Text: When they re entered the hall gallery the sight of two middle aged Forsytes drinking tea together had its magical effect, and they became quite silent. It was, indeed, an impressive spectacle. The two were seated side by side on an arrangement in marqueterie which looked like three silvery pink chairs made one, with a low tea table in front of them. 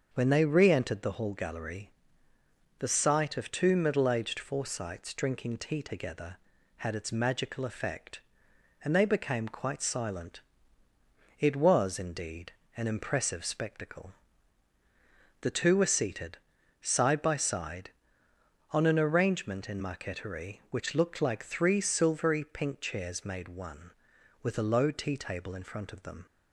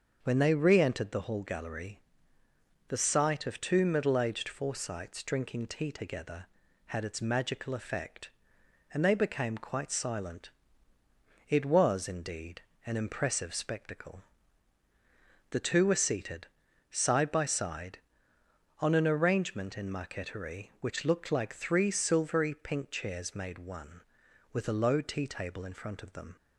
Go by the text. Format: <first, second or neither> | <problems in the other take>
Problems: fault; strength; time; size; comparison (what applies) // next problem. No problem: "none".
neither | starts louder than the rest; the same in both // pauses between "gallery" and "the"; noticeable; the same in both // pauses between "seated" and "side"; the same in both